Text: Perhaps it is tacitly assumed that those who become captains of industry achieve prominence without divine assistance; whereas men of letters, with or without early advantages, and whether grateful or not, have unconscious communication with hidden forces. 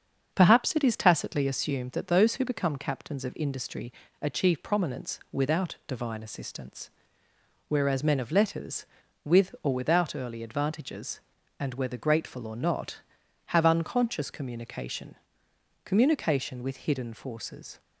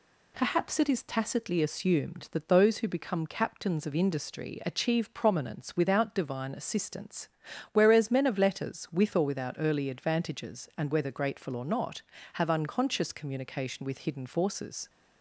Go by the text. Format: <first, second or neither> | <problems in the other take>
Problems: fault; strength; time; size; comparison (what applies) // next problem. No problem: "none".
second | starts louder than the rest; until 1.3 s; 7 dB // pauses between "industry" and "achieve"; slight; at 3.9 s; 0.30 s long // says "communication" twice; at 15.8 s